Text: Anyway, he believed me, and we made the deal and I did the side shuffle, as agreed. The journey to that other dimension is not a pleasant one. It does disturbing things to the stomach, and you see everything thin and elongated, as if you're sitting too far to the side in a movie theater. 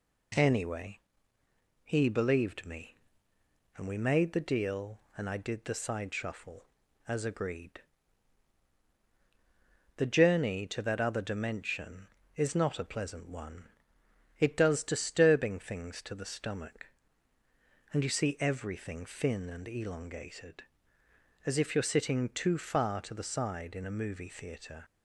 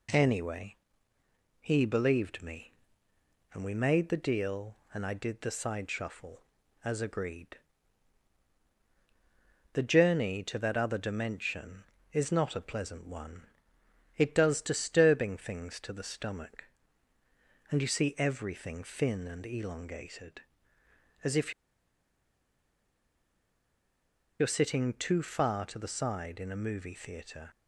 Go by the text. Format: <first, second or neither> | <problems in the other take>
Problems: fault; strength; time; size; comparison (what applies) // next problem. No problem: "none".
first | pauses between "if" and "you're"; strong; at 21.5 s; 2.8 s long